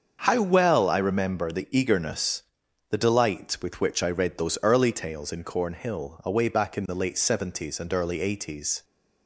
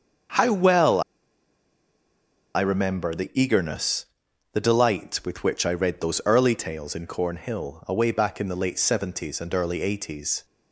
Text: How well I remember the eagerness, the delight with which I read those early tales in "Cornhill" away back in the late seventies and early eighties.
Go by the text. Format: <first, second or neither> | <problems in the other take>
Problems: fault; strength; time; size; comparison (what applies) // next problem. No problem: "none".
first | starts louder than the rest; until 2.8 s; 7 dB; also in the first // pauses between "well" and "I"; strong; at 1.0 s; 1.5 s long